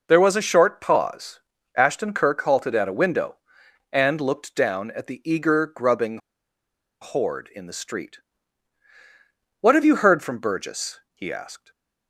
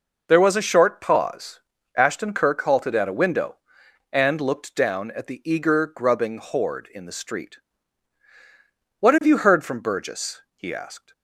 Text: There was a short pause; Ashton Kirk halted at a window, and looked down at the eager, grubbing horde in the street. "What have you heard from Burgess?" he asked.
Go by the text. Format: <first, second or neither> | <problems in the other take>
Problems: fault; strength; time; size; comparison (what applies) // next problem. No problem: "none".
second | pauses between "grubbing" and "horde"; noticeable; at 6.1 s; 0.83 s long // stays silent after the last word; slight; from 11.5 s on; 0.5 s long